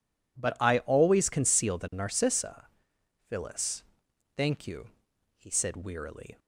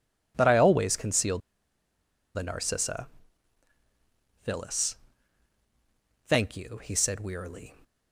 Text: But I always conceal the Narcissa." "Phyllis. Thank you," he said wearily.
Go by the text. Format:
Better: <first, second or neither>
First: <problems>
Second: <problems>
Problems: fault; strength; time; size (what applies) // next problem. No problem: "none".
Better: first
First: none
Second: pauses between "conceal" and "the"; noticeable; at 1.3 s; 0.97 s long